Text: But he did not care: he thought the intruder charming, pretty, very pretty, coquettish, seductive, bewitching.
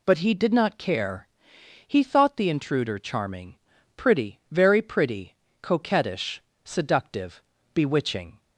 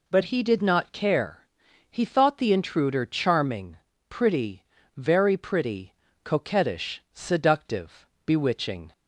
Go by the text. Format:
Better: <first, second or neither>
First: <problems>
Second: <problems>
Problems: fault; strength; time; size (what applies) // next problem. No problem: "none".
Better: neither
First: none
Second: none